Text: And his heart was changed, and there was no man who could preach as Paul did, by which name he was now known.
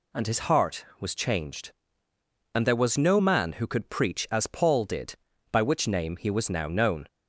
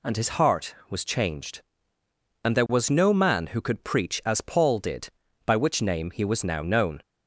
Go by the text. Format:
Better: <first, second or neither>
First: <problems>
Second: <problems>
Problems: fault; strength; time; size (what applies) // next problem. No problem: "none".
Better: neither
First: none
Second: none